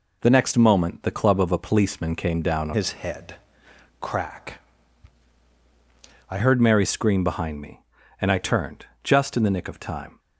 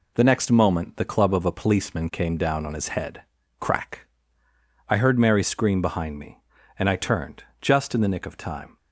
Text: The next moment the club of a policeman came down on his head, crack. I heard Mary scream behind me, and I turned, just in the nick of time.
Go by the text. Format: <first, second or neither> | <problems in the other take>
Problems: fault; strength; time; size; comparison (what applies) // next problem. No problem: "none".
second | changes voice from "his" to "I"; from 2.7 to 6.3 s; 3.6 s long